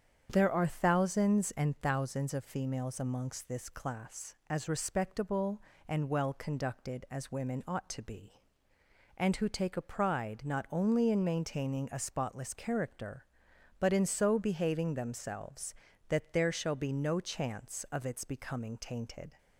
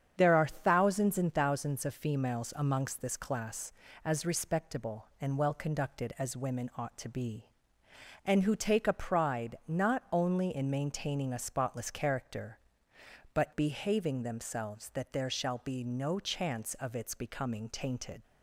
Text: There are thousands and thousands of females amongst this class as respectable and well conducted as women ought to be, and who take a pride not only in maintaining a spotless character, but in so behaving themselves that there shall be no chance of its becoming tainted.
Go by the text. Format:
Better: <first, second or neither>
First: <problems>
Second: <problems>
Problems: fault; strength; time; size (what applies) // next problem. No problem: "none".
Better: first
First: starts louder than the rest; strong; until 1.3 s; 8 dB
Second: starts louder than the rest; strong; until 1.1 s; 8 dB // skips "in so"; at 13.5 s